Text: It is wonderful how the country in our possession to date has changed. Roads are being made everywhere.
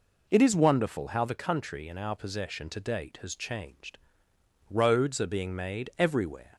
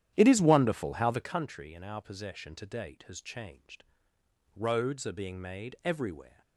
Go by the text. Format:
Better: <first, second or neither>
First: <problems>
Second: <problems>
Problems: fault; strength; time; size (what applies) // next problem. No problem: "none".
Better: first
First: none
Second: starts louder than the rest; strong; until 1.5 s; 11 dB